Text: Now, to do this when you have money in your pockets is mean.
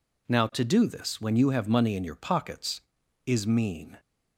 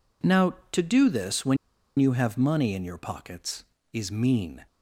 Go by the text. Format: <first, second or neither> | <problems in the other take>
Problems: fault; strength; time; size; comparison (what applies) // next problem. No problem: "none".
first | pauses between "when" and "you"; at 1.5 s; 0.41 s long